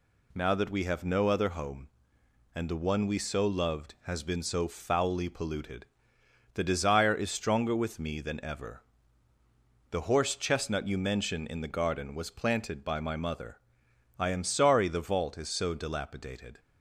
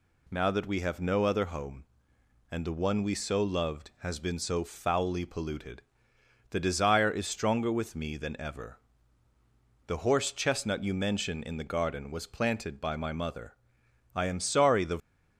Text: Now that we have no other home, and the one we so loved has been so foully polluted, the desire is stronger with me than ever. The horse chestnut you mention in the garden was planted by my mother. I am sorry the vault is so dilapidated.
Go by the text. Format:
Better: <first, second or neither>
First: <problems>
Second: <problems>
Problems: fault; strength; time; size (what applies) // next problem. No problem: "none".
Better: first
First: none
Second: stops before "vault is so dilapidated"; at 14.9 s